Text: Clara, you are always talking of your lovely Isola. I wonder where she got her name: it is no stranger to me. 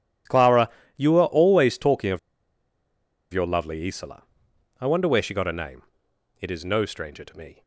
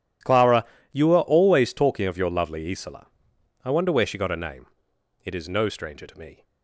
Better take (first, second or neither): second